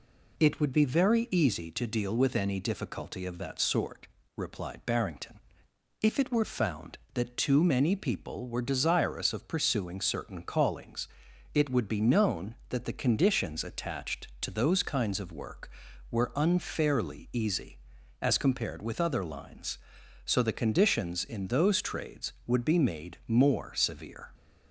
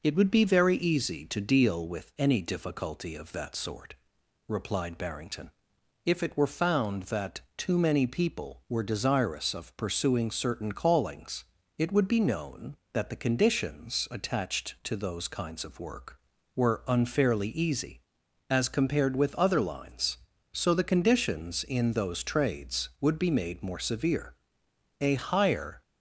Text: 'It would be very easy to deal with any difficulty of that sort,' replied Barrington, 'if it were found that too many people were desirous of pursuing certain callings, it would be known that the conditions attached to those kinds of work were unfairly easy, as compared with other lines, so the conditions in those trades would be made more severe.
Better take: first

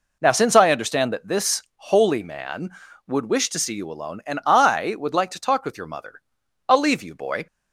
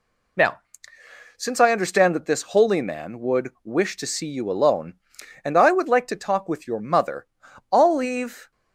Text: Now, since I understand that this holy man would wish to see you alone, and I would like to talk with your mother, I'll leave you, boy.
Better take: first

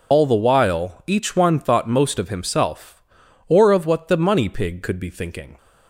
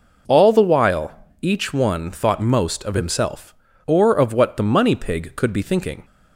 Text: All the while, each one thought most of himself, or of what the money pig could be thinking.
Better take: second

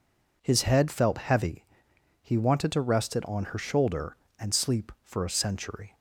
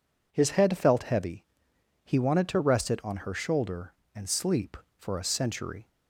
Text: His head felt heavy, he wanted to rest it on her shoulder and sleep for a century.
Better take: neither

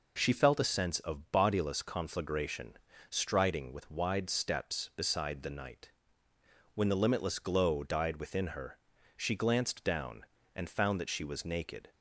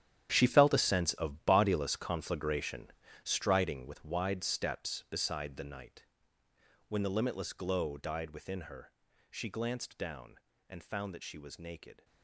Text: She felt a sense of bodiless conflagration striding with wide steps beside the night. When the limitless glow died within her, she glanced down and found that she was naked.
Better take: first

